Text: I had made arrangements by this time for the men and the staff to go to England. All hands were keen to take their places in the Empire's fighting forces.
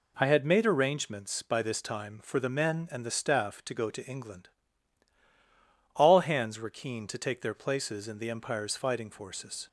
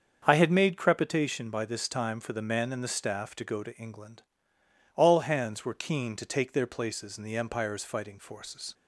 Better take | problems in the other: first | starts louder than the rest; until 1.2 s; 7 dB // says "crepitation" for "arrangements"; at 0.7 s

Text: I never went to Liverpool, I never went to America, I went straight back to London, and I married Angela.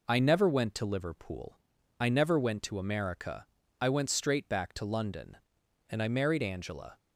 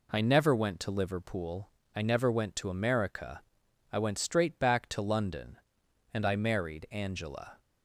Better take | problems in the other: neither | none

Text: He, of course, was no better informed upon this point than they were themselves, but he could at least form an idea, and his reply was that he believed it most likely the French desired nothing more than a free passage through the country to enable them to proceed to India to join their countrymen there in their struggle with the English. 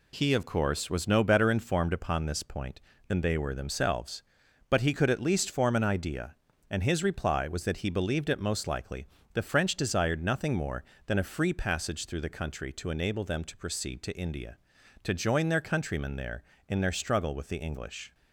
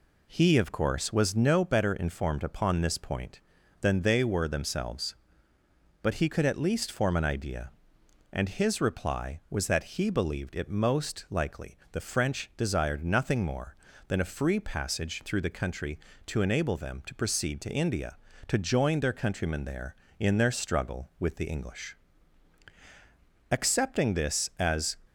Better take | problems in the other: first | pauses between "likely" and "the"; slight; at 11.7 s; 0.16 s long; slight in the first // goes on to say "Accepting this as"; from 23.4 s on; 1.5 s long

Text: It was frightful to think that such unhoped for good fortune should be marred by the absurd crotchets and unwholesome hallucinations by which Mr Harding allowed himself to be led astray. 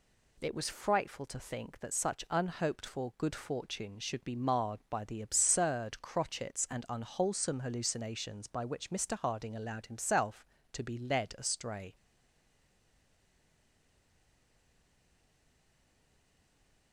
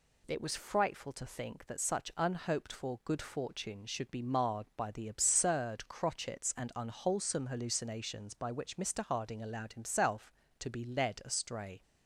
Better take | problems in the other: second | stays silent after the last word; strong; from 11.9 s on; 5.0 s long

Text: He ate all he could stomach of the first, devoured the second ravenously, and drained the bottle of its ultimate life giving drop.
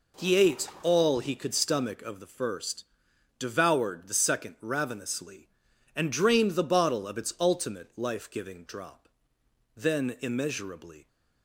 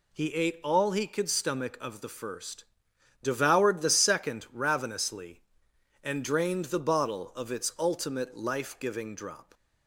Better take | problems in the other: second | goes on to say "Then immeasurably"; from 9.7 s on; 1.3 s long

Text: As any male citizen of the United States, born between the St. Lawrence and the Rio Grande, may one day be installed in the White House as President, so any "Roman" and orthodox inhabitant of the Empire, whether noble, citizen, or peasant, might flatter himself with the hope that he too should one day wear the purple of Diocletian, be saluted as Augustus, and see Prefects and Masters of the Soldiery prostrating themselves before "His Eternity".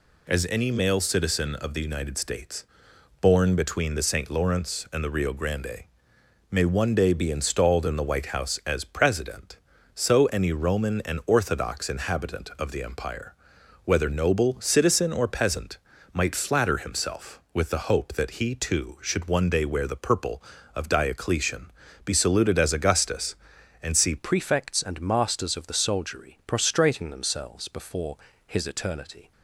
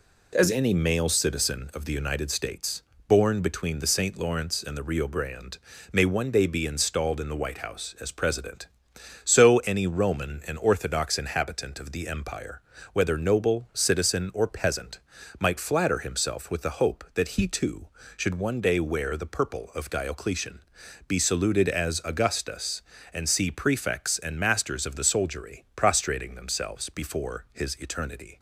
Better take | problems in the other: second | changes voice at "Prefects"; from 24.1 s on; 5.2 s long // pauses between "before" and "His"; slight; at 28.1 s; 0.28 s long

